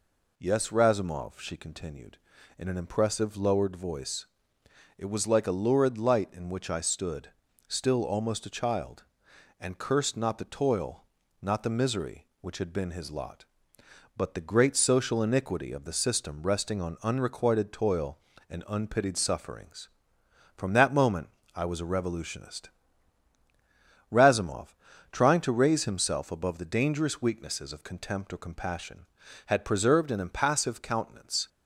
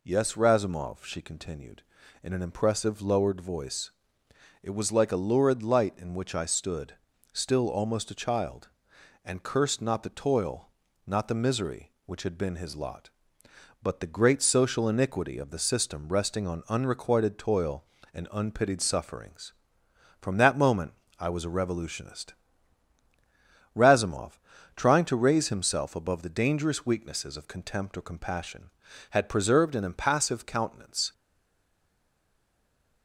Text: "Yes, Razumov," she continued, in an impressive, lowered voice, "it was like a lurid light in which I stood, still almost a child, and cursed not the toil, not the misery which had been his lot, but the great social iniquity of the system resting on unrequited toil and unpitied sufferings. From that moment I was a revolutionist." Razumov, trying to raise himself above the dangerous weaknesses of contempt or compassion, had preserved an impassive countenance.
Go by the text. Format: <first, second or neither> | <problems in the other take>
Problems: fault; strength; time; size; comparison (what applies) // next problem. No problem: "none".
first | pauses between "moment" and "I"; slight; at 20.9 s; 0.24 s long; slight in the first // stays silent after the last word; noticeable; from 31.1 s on; 1.9 s long